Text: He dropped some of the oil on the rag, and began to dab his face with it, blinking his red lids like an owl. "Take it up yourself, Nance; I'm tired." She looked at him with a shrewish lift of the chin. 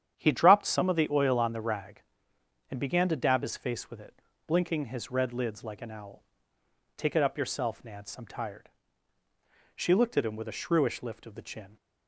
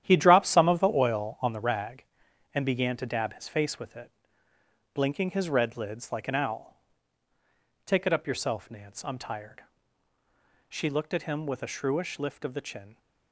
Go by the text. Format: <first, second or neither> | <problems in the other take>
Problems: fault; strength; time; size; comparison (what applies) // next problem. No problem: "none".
first | gets quieter; strong; throughout; 10.5 dB // starts louder than the rest; strong; until 1.0 s; 11 dB; strong in the first